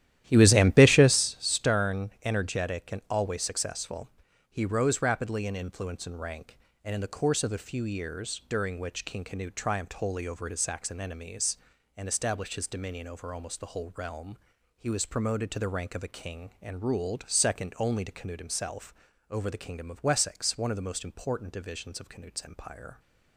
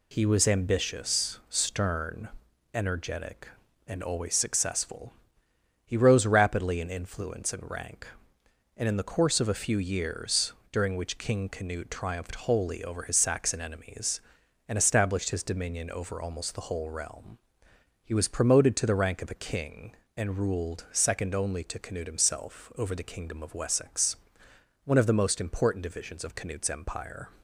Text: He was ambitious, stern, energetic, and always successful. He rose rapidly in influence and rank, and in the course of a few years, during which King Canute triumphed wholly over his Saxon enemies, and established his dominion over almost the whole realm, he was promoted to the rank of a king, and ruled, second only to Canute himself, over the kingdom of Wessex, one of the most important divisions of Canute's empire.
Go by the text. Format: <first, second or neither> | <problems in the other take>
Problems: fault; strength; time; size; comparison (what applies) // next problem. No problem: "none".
second | starts louder than the rest; strong; until 1.3 s; 12.5 dB